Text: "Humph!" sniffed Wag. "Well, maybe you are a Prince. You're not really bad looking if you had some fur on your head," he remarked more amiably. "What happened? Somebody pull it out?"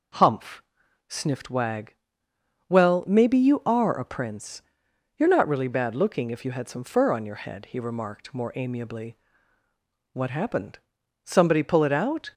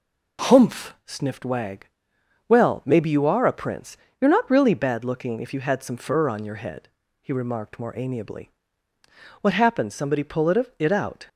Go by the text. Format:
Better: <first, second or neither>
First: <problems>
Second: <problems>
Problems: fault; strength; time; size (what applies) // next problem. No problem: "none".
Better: first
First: none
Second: says "it" twice; at 10.7 s